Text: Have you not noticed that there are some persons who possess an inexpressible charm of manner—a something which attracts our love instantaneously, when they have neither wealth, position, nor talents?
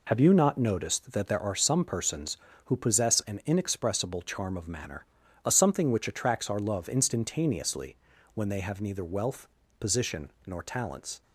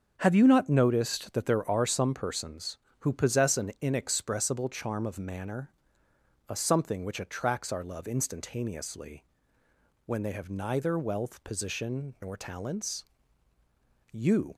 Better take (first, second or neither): first